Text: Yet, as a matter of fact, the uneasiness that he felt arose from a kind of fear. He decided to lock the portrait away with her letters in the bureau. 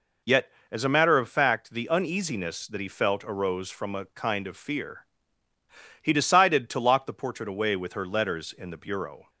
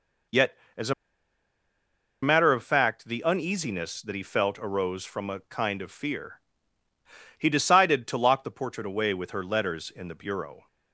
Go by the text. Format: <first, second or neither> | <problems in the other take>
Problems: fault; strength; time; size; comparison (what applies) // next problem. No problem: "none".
first | pauses between "a" and "matter"; strong; at 0.9 s; 1.2 s long